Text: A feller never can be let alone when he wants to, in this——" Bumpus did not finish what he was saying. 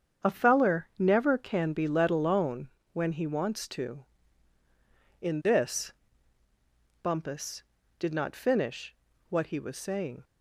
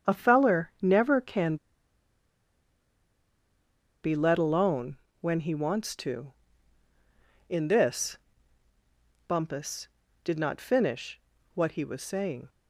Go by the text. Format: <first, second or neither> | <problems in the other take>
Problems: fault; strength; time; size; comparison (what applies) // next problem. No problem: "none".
first | starts louder than the rest; strong; until 1.1 s; 7.5 dB; strong in the first // pauses between "can" and "be"; strong; at 1.5 s; 2.4 s long // pauses between "alone" and "when"; slight; at 4.9 s; 0.24 s long; slight in the first // pauses between "finish" and "what"; slight; at 11.2 s; 0.34 s long; slight in the first